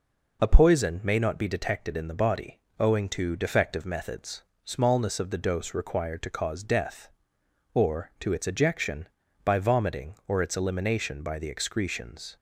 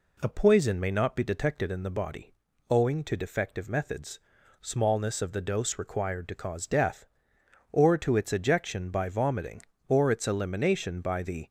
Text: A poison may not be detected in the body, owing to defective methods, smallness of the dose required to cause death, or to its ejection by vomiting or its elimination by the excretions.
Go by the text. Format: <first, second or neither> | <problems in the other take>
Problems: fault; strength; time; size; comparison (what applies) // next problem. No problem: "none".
first | stops before "excretions"; at 11.4 s